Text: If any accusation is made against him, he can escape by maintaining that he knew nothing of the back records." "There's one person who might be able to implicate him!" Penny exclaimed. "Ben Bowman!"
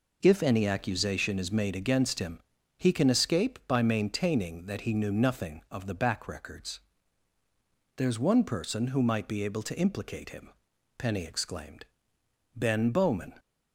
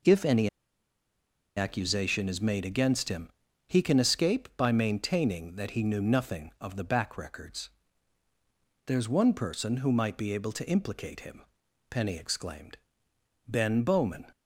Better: first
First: none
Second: pauses between "any" and "accusation"; at 0.4 s; 1.0 s long

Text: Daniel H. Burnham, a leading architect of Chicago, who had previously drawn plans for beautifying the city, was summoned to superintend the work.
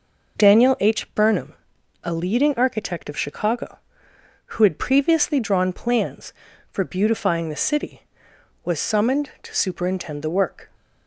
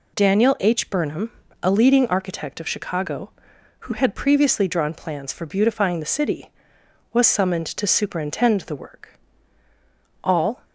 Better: first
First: none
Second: goes on to say "All"; slight; from 10.2 s on; 0.42 s long

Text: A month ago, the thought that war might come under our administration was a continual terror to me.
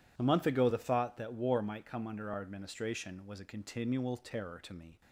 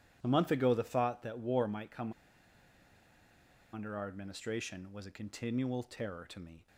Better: first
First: none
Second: pauses between "come" and "under"; strong; at 2.1 s; 1.6 s long

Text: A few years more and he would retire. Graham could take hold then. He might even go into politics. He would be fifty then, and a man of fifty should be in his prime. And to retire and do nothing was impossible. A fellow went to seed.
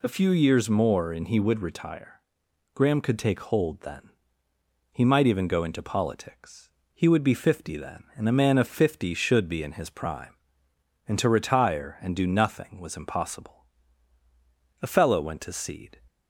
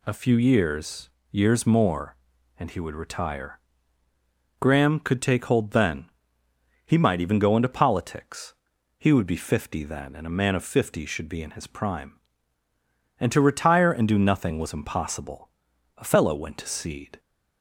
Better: first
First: none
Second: says "years" twice; at 1.2 s

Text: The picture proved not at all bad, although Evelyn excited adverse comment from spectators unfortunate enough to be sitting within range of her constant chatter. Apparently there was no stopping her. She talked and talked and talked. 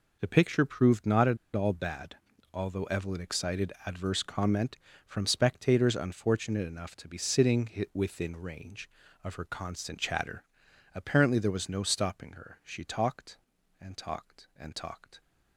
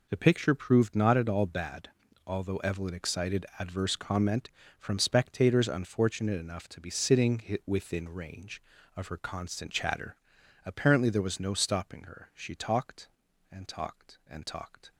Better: second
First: pauses between "at" and "all"; slight; at 1.3 s; 0.19 s long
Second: none

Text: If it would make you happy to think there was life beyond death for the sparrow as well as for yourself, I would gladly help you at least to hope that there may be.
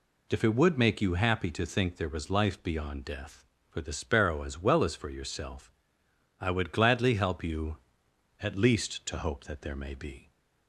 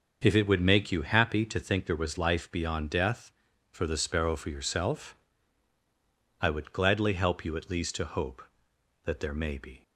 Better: first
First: none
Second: starts louder than the rest; until 1.2 s; 6.5 dB // skips "as well as"; at 4.3 s

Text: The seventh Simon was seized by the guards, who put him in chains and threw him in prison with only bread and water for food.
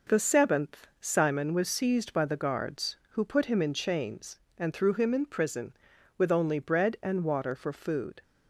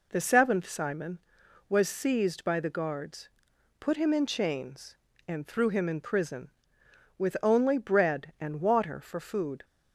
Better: first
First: none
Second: skips "who"; at 3.5 s

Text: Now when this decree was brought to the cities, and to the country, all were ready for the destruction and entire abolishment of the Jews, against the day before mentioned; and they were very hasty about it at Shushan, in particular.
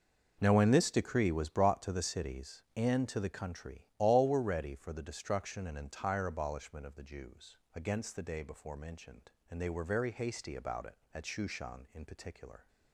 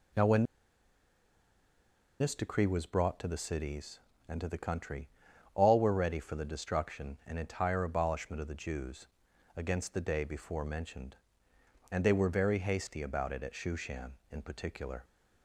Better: first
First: none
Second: pauses between "when" and "this"; strong; at 0.4 s; 1.7 s long

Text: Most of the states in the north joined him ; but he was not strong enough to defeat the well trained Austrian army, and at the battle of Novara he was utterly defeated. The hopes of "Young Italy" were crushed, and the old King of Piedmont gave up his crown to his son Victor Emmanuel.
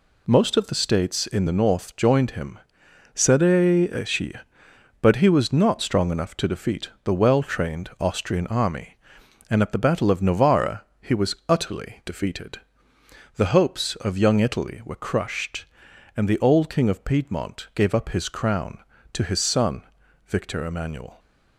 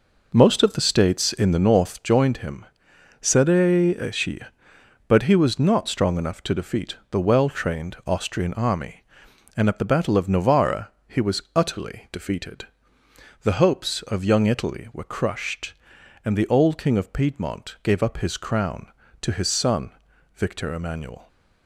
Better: first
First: pauses between "but" and "he"; strong; at 3.4 s; 1.7 s long // pauses between "Novara" and "he"; slight; at 10.8 s; 0.16 s long // pauses between "son" and "Victor"; at 19.8 s; 0.42 s long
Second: starts louder than the rest; noticeable; until 2.2 s; 4.5 dB // pauses between "but" and "he"; strong; at 3.4 s; 1.7 s long // pauses between "Novara" and "he"; slight; at 10.9 s; 0.16 s long // pauses between "son" and "Victor"; at 19.9 s; 0.42 s long

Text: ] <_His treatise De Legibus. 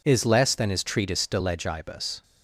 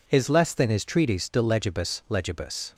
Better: first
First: none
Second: says "Legibus" twice; at 2.1 s

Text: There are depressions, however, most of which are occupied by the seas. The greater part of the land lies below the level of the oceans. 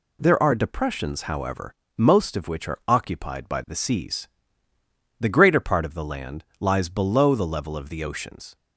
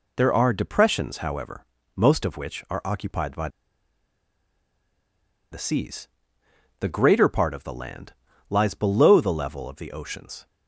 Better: first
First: pauses between "land" and "lies"; slight; at 6.4 s; 0.16 s long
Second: pauses between "by" and "the"; strong; at 3.4 s; 2.0 s long // pauses between "land" and "lies"; slight; at 8.1 s; 0.34 s long

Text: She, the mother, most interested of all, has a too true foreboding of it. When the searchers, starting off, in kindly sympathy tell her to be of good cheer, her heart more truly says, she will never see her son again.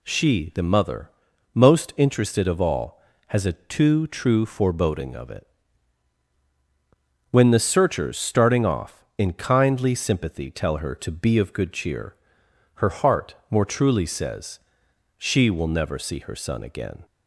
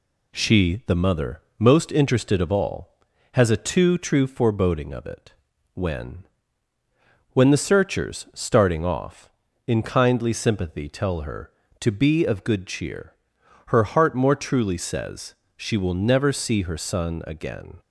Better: first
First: none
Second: says "When" twice; at 7.3 s

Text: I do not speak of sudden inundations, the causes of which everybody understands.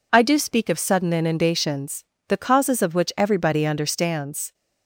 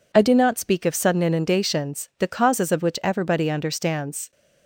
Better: second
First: skips "not"; at 0.3 s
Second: none

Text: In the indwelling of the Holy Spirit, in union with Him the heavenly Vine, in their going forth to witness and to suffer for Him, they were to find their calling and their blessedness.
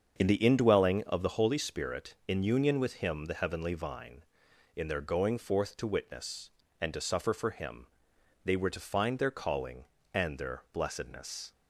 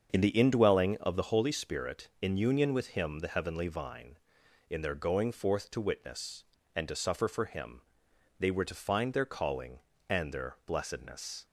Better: neither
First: starts louder than the rest; until 1.1 s; 7 dB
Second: starts louder than the rest; until 1.1 s; 7 dB

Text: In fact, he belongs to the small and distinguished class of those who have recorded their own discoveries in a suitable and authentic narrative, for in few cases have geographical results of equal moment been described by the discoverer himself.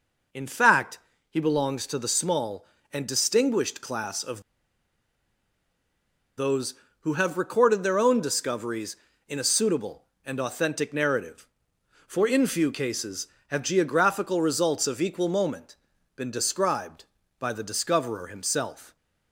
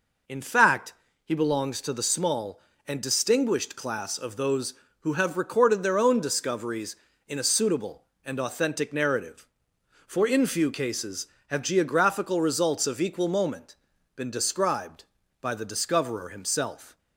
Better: second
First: pauses between "of" and "those"; strong; at 4.4 s; 1.9 s long // pauses between "moment" and "been"; at 15.7 s; 0.40 s long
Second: pauses between "moment" and "been"; at 13.7 s; 0.40 s long

